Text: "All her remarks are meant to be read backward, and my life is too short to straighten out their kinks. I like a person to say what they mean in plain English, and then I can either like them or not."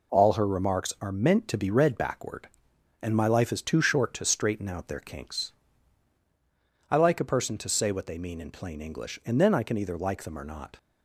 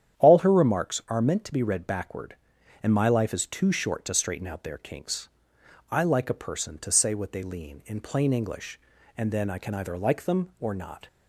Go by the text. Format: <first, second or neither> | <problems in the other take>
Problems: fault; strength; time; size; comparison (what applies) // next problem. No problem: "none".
first | starts louder than the rest; strong; until 1.2 s; 9.5 dB // says "lean" for "mean"; at 7.4 s